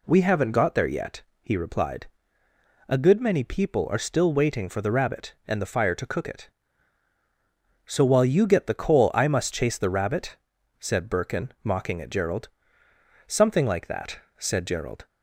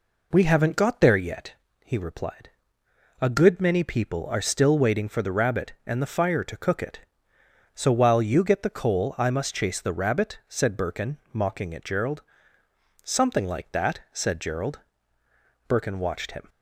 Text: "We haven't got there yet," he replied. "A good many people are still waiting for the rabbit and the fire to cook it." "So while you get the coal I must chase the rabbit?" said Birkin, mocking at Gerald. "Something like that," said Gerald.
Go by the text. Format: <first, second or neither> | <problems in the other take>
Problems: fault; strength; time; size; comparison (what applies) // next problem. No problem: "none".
first | goes on to say "Birkin watched him"; noticeable; from 15.6 s on; 0.82 s long